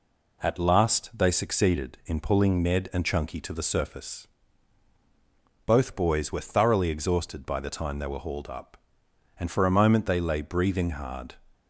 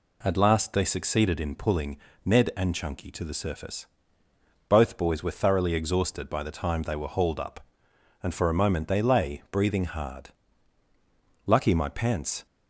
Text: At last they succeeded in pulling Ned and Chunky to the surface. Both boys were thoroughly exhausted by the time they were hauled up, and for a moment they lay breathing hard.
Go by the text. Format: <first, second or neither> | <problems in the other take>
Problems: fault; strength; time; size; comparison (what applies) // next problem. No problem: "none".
first | pauses between "pulling" and "Ned"; slight; at 1.9 s; 0.26 s long // goes on to say "Lucky my pants"; noticeable; from 11.4 s on; 0.98 s long